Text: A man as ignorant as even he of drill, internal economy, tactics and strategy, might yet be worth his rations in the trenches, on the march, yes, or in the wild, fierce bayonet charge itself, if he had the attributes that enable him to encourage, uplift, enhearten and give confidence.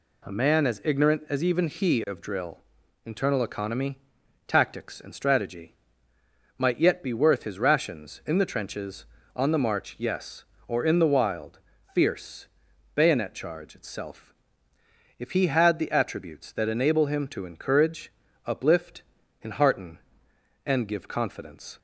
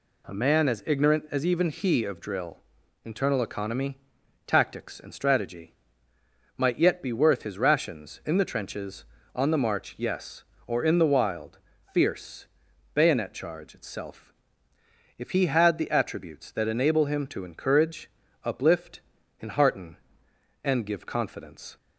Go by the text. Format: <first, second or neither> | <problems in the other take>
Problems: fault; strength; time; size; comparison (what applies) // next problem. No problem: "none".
neither | pauses between "fierce" and "bayonet"; noticeable; the same in both